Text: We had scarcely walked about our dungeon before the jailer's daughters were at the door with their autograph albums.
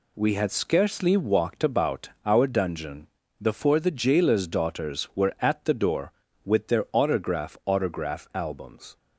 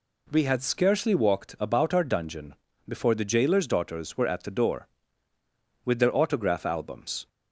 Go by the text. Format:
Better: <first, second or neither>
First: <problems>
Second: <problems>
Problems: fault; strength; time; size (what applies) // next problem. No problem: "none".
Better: second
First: pauses between "about" and "our"; slight; at 2.0 s; 0.16 s long // pauses between "dungeon" and "before"; slight; at 3.0 s; 0.34 s long // says "autograph" twice; at 7.6 s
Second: pauses between "dungeon" and "before"; slight; at 2.5 s; 0.32 s long